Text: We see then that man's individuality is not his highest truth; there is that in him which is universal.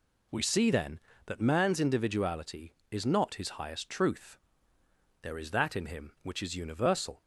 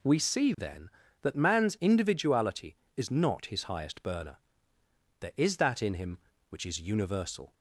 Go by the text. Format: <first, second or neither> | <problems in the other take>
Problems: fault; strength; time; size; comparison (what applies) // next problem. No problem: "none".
first | says "burner" for "truth"; at 4.0 s